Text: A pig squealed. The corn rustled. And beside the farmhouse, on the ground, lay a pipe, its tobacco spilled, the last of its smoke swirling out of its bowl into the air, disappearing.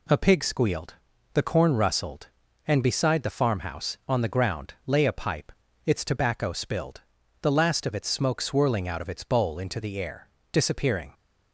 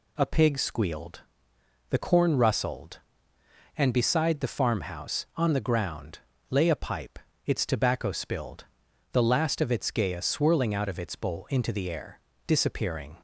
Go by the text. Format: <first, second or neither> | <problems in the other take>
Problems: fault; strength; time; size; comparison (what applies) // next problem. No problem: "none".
first | says "gaya" for "smoke"; at 9.9 s